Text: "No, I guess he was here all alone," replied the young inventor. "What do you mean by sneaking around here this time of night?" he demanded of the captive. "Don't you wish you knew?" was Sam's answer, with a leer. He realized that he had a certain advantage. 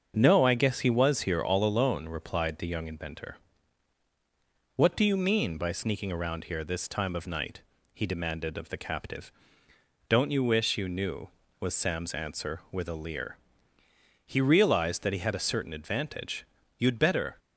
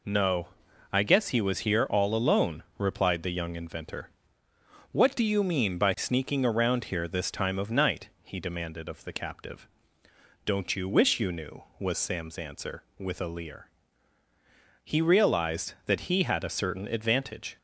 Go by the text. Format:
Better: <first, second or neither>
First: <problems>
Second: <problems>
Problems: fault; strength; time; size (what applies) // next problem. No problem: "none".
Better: second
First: starts louder than the rest; until 1.1 s; 7 dB // goes on to say "You'd better"; from 16.7 s on; 0.60 s long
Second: none